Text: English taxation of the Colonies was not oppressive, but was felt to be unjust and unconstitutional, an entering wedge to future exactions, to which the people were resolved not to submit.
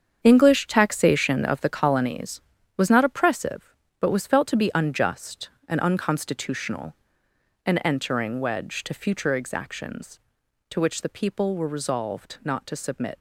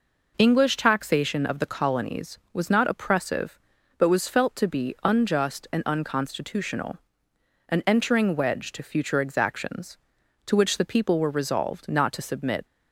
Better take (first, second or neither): second